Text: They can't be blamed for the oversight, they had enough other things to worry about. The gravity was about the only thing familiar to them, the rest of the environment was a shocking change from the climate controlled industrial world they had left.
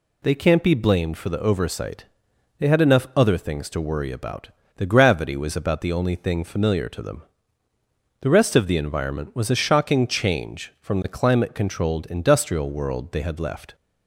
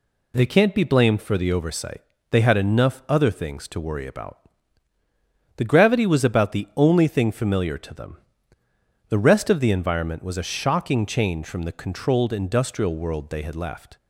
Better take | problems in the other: first | skips "climate"; at 11.7 s

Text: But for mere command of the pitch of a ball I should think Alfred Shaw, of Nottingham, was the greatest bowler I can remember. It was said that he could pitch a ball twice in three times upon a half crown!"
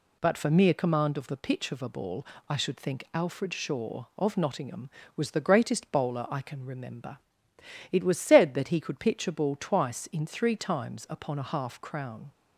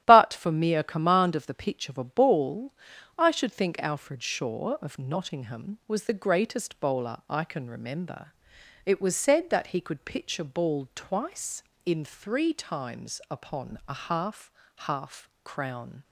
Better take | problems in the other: first | starts louder than the rest; strong; until 1.0 s; 12.5 dB // pauses between "ball" and "I"; at 2.7 s; 0.44 s long; slight in the first // says "half" twice; at 14.7 s

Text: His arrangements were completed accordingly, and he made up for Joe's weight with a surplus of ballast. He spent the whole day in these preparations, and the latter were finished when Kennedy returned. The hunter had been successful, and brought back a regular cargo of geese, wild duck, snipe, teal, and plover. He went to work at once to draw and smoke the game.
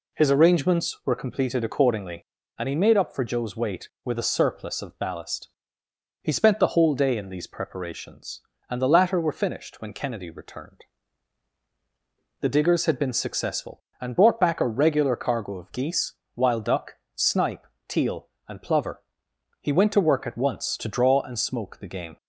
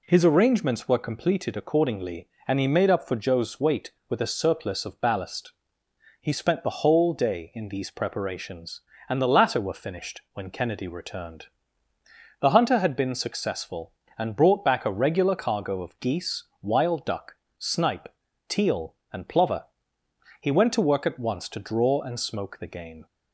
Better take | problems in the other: second | says "diggers" for "hunter"; at 12.4 s

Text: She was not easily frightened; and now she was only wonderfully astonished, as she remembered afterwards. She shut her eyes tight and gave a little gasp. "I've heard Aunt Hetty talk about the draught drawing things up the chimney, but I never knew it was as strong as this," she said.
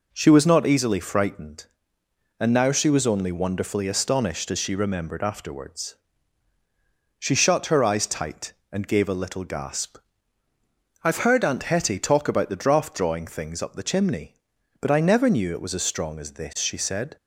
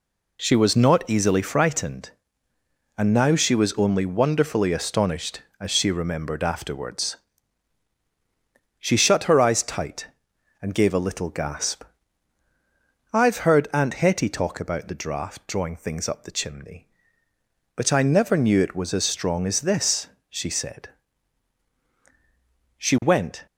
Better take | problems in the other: first | goes on to say "She went"; noticeable; from 22.7 s on; 0.67 s long

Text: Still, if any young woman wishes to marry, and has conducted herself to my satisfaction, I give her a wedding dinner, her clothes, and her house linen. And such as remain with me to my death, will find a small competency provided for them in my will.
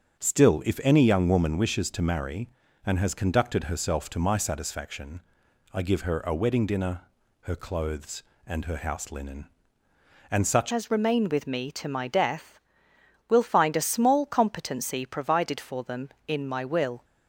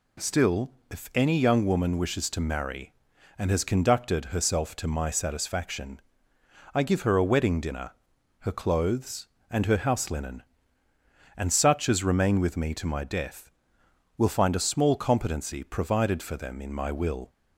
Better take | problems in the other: second | starts louder than the rest; until 1.2 s; 7 dB // changes voice at "as"; from 10.7 s on; 6.3 s long

